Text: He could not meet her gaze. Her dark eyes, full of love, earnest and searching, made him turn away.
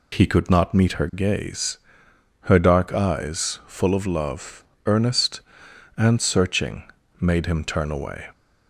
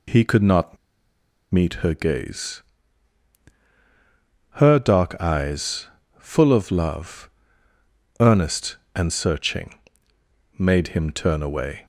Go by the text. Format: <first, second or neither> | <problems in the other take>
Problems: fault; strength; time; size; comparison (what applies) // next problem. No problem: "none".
first | pauses between "not" and "meet"; noticeable; at 0.7 s; 0.76 s long